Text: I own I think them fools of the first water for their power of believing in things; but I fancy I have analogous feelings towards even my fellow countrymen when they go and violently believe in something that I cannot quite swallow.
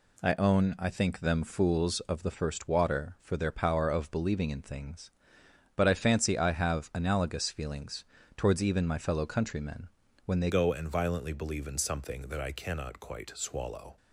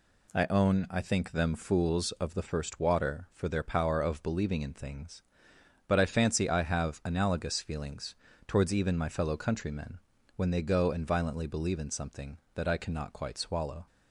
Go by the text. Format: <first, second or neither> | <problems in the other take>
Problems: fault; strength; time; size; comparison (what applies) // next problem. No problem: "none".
second | pauses between "feelings" and "towards"; slight; at 8.0 s; 0.32 s long; slight in the second // pauses between "countrymen" and "when"; slight; at 9.8 s; 0.36 s long; slight in the second // changes voice at "go"; from 10.4 s on; 3.5 s long